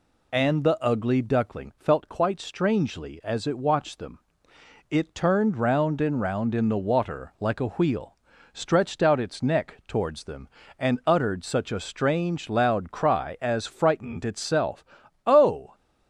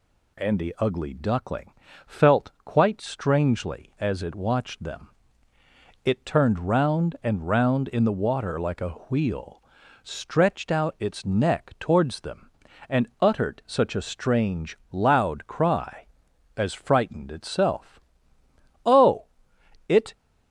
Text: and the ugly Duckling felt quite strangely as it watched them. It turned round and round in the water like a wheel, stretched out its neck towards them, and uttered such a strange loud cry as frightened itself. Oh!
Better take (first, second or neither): first